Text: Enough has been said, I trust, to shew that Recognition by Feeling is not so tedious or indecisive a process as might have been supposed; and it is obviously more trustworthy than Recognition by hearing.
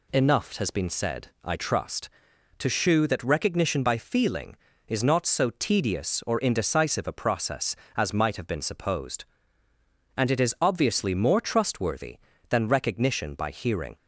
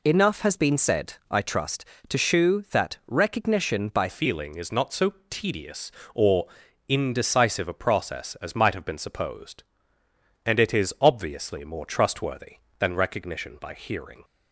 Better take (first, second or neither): first